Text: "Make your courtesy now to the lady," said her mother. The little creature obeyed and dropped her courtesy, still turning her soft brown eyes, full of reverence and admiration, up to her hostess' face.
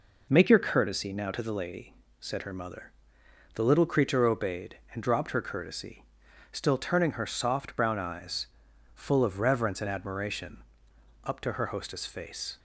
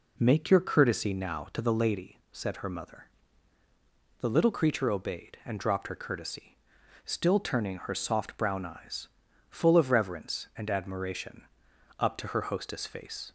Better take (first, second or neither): neither